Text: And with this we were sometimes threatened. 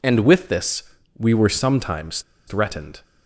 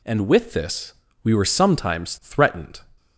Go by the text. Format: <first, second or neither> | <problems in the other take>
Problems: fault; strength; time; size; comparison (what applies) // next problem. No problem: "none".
second | pauses between "this" and "we"; slight; at 0.8 s; 0.34 s long; slight in the second // pauses between "sometimes" and "threatened"; slight; at 2.2 s; 0.27 s long